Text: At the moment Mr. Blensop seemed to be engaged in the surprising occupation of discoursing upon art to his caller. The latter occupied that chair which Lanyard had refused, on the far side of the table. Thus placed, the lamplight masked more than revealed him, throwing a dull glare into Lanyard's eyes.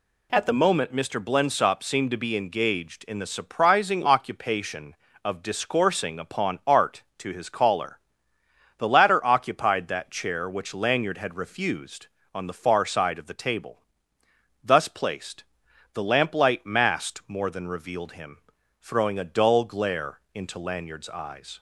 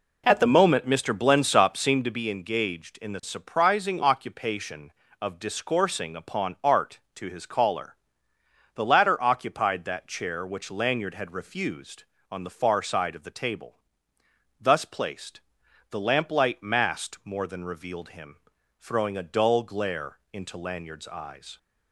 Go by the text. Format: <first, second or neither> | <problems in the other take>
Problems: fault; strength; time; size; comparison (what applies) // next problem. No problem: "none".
first | starts louder than the rest; until 2.1 s; 3.5 dB // pauses between "glare" and "into"; slight; at 20.1 s; 0.16 s long; slight in the first